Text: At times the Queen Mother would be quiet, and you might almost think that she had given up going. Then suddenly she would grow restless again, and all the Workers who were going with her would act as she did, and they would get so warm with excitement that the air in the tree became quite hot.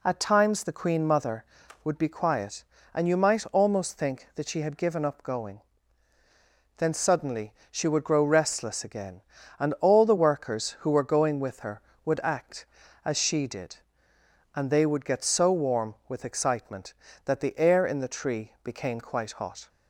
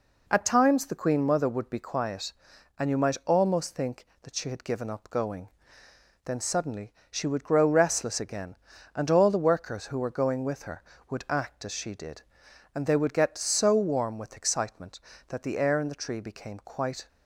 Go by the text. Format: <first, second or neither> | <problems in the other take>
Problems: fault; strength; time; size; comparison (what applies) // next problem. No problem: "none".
first | pauses between "suddenly" and "she"; slight; at 6.9 s; 0.18 s long; slight in the first // stops before "hot"; at 17.0 s